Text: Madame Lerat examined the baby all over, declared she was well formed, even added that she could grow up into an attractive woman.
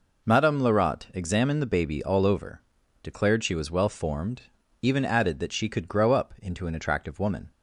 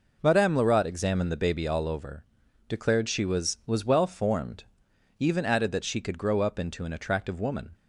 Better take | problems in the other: first | says "was" twice; at 3.6 s

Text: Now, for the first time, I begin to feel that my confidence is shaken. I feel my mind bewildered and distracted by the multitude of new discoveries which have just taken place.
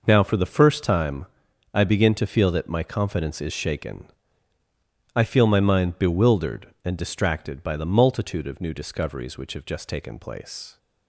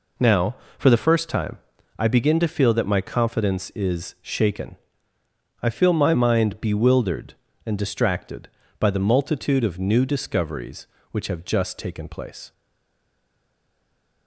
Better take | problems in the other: first | stays silent after the last word; noticeable; from 12.5 s on; 1.7 s long

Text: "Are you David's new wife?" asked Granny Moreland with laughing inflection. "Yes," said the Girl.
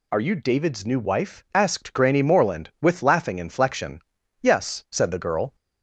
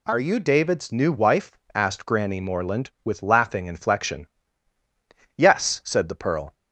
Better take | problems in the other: first | says "Pearl" for "Girl"; at 6.1 s

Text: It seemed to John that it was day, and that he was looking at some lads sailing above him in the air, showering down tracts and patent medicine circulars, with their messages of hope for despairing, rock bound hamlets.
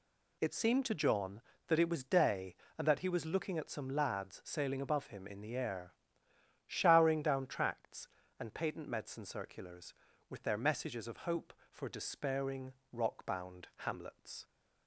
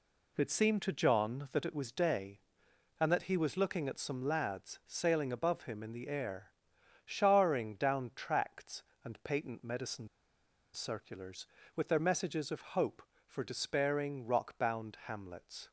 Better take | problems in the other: first | pauses between "medicine" and "circulars"; noticeable; at 10.0 s; 0.66 s long

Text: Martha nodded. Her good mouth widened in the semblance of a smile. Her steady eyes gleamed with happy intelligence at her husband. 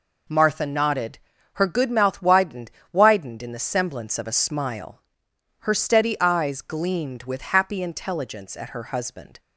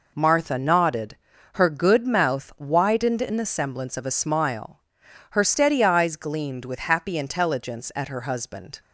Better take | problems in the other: second | says "widened" twice; at 2.9 s

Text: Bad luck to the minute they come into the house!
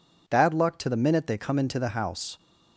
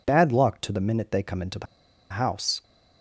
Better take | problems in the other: first | pauses between "the" and "house"; noticeable; at 1.6 s; 0.46 s long

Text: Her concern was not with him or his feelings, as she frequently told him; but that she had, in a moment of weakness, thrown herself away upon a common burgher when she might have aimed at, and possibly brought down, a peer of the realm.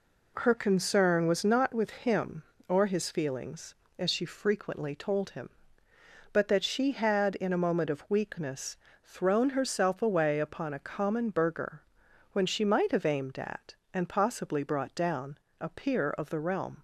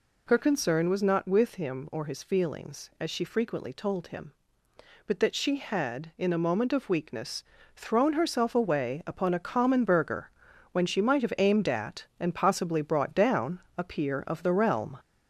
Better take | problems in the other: first | gets louder; slight; throughout; 3.5 dB // pauses between "burgher" and "when"; at 10.2 s; 0.44 s long; noticeable in the first

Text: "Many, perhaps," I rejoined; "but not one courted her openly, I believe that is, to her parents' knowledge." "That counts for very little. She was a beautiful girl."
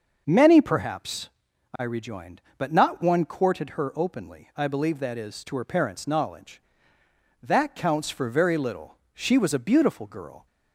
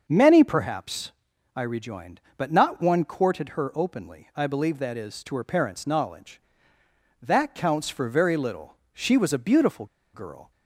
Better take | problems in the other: first | starts louder than the rest; noticeable; until 1.0 s; 6 dB; noticeable in the first // pauses between "beautiful" and "girl"; slight; at 9.8 s; 0.28 s long

